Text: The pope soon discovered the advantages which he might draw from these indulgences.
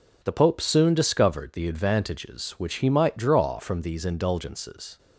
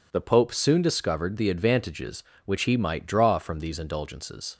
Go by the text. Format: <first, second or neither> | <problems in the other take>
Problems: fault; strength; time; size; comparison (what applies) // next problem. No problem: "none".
neither | none